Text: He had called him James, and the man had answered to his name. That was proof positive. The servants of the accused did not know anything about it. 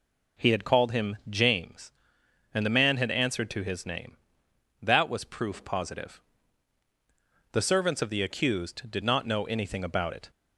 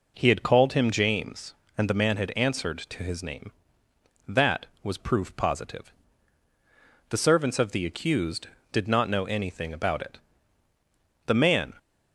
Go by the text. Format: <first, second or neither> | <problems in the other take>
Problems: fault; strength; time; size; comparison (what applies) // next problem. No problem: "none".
first | goes on to say "The man"; slight; from 11.2 s on; 0.46 s long